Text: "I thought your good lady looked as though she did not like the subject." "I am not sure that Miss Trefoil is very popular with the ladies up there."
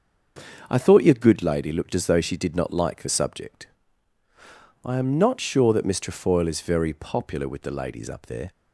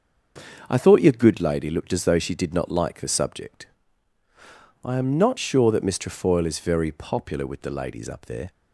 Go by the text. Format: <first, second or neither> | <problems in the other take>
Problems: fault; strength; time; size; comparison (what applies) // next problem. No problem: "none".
neither | starts louder than the rest; the same in both